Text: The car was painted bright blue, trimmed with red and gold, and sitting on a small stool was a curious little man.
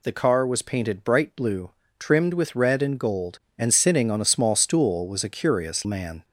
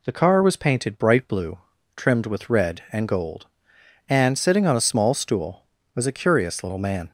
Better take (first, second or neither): second